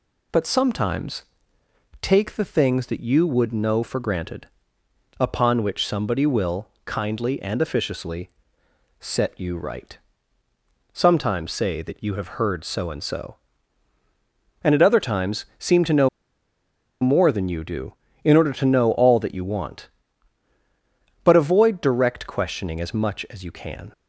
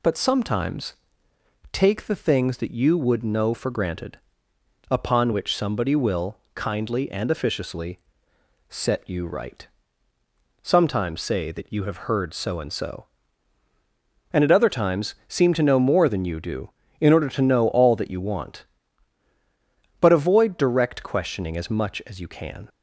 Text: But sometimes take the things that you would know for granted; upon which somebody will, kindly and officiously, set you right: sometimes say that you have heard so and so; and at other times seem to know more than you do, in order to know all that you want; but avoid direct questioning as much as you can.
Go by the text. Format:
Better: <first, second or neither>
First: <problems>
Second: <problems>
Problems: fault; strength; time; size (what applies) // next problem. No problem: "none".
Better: second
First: pauses between "sometimes" and "take"; noticeable; at 1.2 s; 0.78 s long // pauses between "know" and "more"; noticeable; at 16.0 s; 0.95 s long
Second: pauses between "sometimes" and "take"; noticeable; at 0.9 s; 0.78 s long